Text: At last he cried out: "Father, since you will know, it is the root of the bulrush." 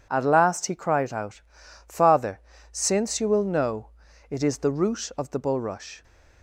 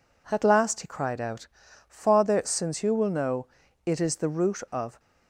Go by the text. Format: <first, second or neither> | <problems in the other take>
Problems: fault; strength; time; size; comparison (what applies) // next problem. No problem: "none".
first | stops before "the bulrush"; at 4.9 s